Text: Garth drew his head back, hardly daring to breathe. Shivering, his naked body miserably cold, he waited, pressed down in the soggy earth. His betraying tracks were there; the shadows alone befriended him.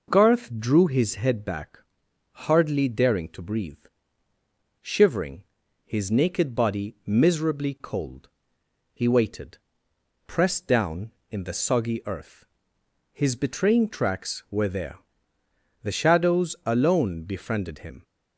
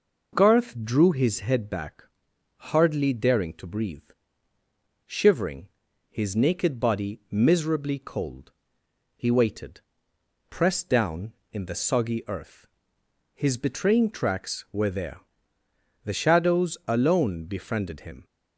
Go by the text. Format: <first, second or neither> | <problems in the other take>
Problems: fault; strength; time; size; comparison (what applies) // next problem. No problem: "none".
neither | none